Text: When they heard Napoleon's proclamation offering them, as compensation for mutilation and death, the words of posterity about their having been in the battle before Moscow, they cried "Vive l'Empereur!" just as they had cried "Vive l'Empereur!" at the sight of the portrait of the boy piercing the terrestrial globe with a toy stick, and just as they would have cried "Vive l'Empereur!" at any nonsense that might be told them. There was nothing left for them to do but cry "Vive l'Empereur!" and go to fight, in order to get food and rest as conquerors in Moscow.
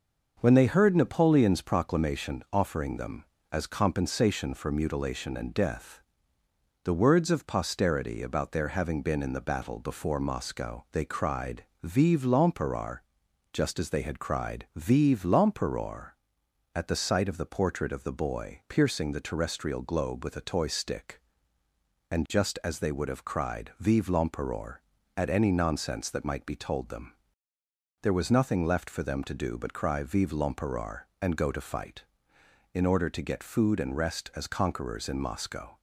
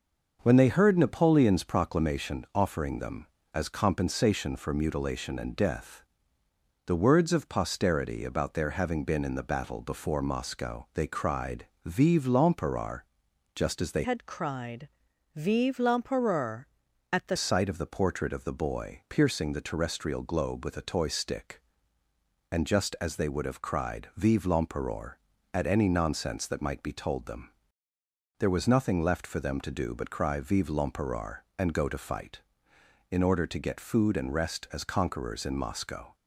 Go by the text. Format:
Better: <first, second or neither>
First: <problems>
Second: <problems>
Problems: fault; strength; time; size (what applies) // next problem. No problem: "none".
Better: first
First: pauses between "cried" and "Vive"; slight; at 11.6 s; 0.18 s long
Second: pauses between "cried" and "Vive"; slight; at 11.6 s; 0.18 s long // changes voice from "had" to "the"; from 14.0 to 17.3 s; 3.3 s long // pauses between "cried" and "Vive"; noticeable; at 14.8 s; 0.46 s long